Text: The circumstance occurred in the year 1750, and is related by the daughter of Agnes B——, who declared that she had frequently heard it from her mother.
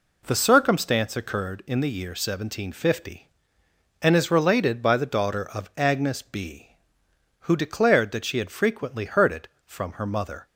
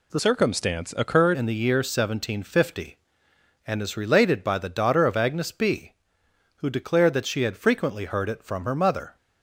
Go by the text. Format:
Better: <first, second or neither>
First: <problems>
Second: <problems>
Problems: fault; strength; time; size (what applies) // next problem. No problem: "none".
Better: first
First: none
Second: changes voice from "circumstance" to "occurred"; from 0.1 to 1.3 s; 1.2 s long